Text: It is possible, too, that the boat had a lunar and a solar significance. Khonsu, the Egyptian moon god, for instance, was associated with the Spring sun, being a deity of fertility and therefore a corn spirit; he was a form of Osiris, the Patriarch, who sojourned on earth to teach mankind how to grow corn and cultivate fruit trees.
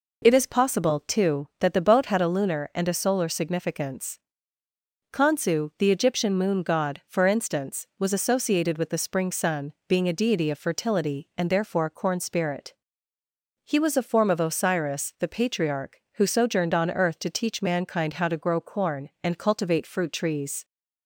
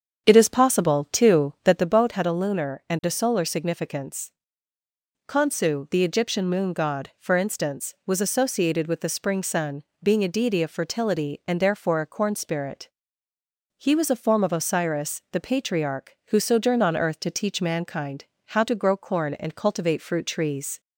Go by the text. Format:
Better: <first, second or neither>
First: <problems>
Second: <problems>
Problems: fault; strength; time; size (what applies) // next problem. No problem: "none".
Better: first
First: none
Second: starts louder than the rest; strong; until 1.9 s; 8 dB // pauses between "mankind" and "how"; slight; at 18.2 s; 0.22 s long